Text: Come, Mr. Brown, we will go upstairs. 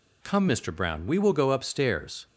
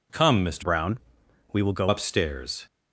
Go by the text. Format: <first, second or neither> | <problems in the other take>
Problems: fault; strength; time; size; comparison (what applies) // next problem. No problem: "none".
first | changes voice from "Brown" to "go"; from 0.6 to 1.8 s; 1.2 s long